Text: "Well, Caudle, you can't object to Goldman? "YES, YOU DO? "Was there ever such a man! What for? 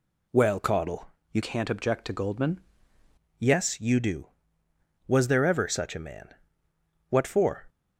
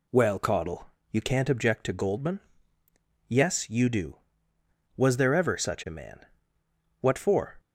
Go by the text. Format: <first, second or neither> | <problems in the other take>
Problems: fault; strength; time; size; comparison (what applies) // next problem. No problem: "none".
second | changes voice from "can't" to "Goldman"; from 1.4 to 2.5 s; 1.1 s long